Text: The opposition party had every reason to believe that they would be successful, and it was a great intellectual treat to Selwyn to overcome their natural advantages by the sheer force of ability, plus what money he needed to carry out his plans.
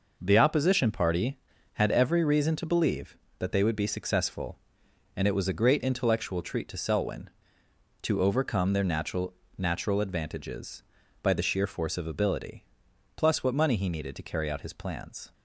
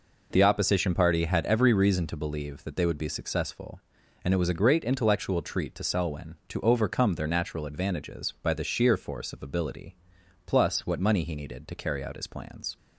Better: second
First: says "natural" twice; at 9.5 s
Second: none

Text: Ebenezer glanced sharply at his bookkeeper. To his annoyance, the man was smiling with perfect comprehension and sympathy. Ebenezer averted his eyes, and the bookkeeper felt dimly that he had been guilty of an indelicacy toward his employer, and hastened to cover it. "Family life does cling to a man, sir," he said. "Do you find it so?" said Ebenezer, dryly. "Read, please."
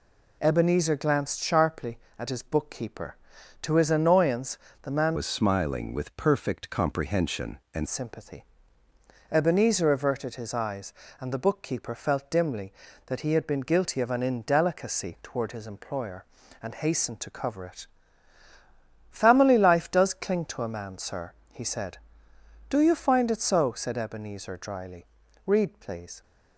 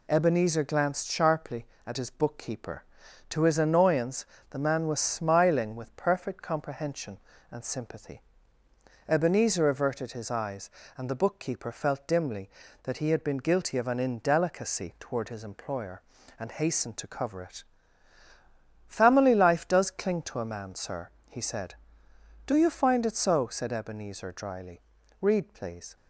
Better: second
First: changes voice from "was" to "and"; from 5.1 to 7.8 s; 2.7 s long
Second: none

